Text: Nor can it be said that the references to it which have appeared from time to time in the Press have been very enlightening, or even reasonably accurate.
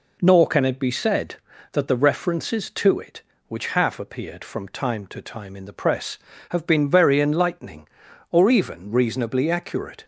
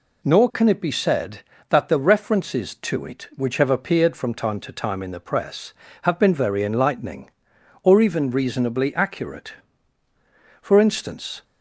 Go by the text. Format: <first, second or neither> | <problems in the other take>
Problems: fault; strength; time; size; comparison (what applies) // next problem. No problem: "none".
first | goes on to say "For instance"; noticeable; from 10.6 s on; 0.82 s long